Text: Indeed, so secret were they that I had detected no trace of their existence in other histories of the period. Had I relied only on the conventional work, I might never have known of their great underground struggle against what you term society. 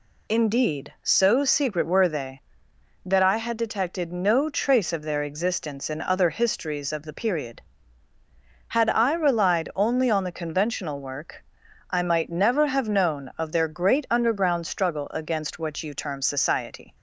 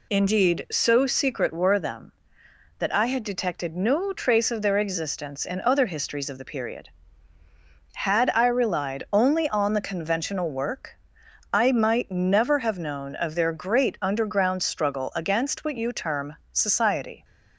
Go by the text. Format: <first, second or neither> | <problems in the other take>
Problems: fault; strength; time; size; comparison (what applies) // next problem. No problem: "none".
first | says "them" for "they"; at 1.7 s // pauses between "term" and "society"; slight; at 16.3 s; 0.16 s long